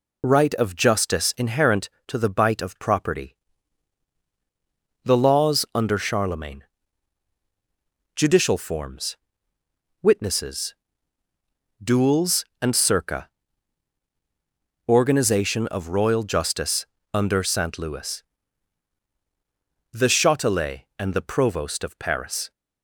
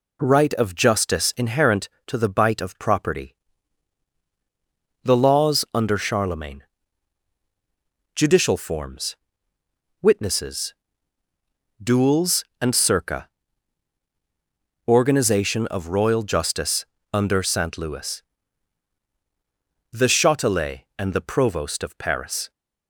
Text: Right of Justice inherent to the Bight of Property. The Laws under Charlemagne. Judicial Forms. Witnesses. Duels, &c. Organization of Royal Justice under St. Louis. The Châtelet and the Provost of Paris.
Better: second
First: loses the start of "Right"; at 0.2 s; 40 ms // pauses between "Justice" and "under"; slight; at 16.8 s; 0.30 s long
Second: pauses between "Justice" and "under"; slight; at 16.8 s; 0.30 s long

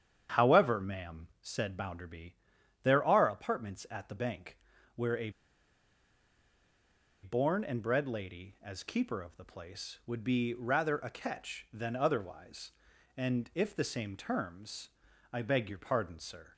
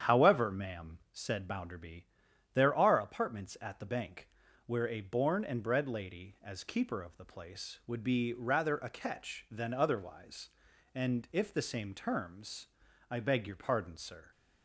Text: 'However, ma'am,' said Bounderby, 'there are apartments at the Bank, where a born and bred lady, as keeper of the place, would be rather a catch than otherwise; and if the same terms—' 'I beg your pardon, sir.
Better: second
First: starts louder than the rest; strong; until 1.5 s; 8.5 dB // pauses between "a" and "born"; strong; at 5.3 s; 1.9 s long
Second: starts louder than the rest; strong; until 1.2 s; 8.5 dB

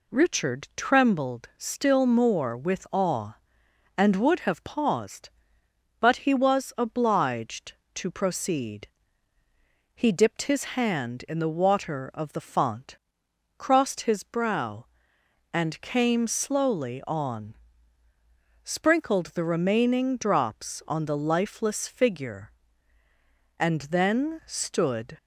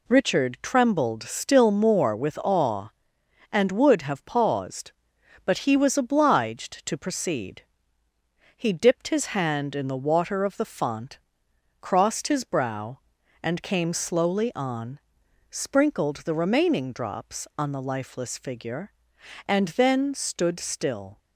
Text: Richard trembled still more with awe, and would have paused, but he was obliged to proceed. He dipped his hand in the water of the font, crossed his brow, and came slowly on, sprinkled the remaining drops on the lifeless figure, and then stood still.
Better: second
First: stops before "still"; at 25.1 s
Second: none

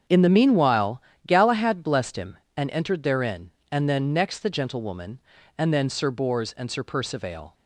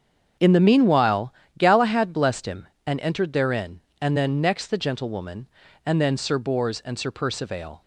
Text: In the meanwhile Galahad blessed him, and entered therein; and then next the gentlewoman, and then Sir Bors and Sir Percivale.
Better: neither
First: starts louder than the rest; strong; until 1.3 s; 8 dB // pauses between "meanwhile" and "Galahad"; slight; at 0.9 s; 0.28 s long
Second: starts louder than the rest; strong; until 1.6 s; 8 dB // pauses between "meanwhile" and "Galahad"; slight; at 1.3 s; 0.28 s long

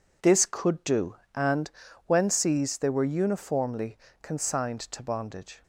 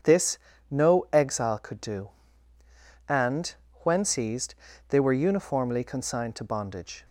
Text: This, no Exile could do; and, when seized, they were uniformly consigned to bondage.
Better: second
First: skips "no Exile"; at 0.4 s // pauses between "uniformly" and "consigned"; slight; at 3.9 s; 0.24 s long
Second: none

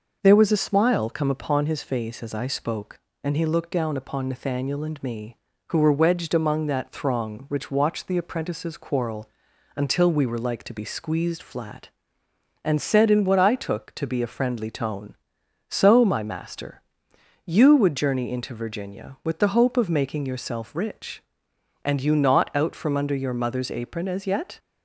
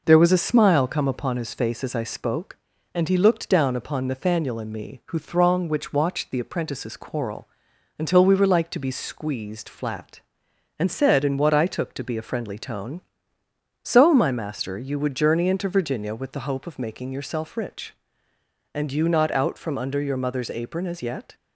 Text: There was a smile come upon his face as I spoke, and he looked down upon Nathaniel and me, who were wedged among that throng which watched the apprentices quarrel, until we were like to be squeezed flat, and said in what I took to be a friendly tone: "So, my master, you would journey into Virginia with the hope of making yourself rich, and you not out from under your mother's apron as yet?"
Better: first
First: none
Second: skips "were wedged among that"; at 5.1 s

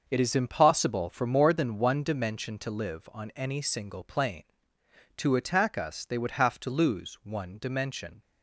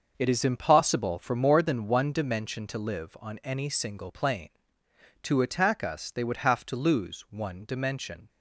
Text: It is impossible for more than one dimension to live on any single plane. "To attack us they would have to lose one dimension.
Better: neither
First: starts louder than the rest; until 1.1 s; 6 dB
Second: starts louder than the rest; until 1.1 s; 6.5 dB

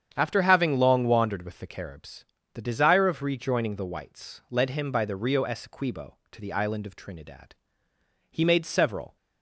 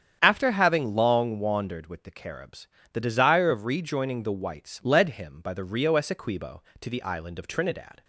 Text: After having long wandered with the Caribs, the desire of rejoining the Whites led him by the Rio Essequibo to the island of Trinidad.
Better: second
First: starts louder than the rest; strong; until 1.1 s; 8 dB // goes on to say "He made several"; noticeable; from 8.3 s on; 0.85 s long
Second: starts louder than the rest; strong; until 1.2 s; 8.5 dB

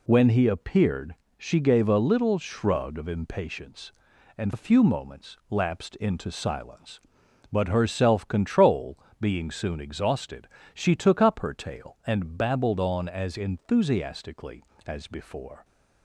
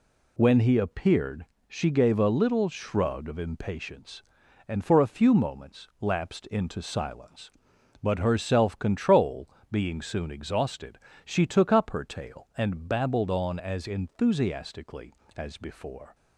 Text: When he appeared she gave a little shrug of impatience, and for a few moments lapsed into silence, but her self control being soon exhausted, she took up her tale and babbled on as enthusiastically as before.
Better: second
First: pauses between "appeared" and "she"; slight; at 1.1 s; 0.22 s long // skips "for"; at 4.5 s // pauses between "control" and "being"; slight; at 8.9 s; 0.22 s long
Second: pauses between "appeared" and "she"; slight; at 1.4 s; 0.22 s long // pauses between "control" and "being"; slight; at 9.4 s; 0.22 s long

